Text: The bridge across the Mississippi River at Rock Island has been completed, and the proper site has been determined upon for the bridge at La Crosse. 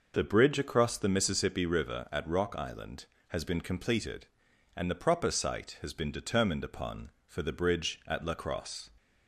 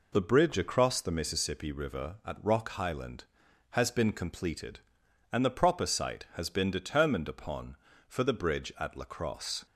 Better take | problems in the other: first | says "Highland" for "Island"; at 2.6 s

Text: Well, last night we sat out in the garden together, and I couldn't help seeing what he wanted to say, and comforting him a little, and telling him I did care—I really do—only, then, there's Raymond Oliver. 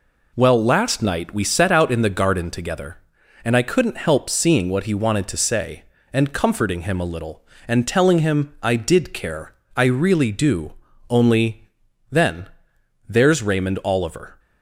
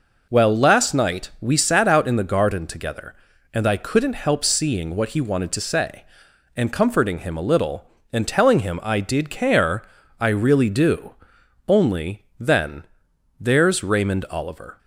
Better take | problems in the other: second | says "set" for "sat"; at 1.4 s

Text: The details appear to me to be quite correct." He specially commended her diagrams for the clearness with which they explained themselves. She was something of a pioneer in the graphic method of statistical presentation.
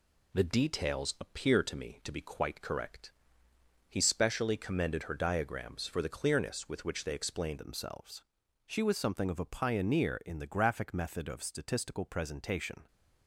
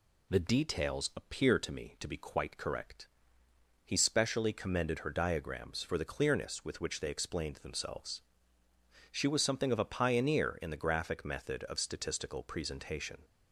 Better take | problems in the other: second | changes voice at "themselves"; from 7.5 s on; 5.3 s long

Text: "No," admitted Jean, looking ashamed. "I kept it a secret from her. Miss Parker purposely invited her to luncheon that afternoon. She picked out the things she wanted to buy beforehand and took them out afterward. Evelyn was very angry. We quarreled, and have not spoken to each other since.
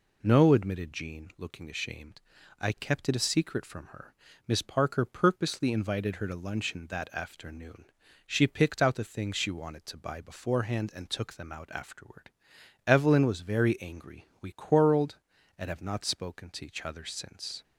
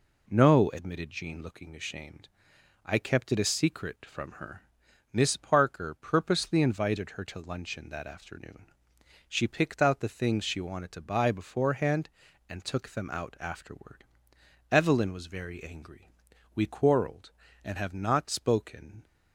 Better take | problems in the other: first | stops before "to each other since"; at 19.0 s

